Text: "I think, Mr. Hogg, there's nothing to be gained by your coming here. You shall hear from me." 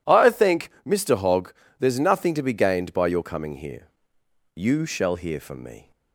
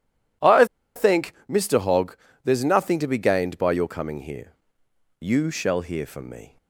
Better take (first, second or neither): first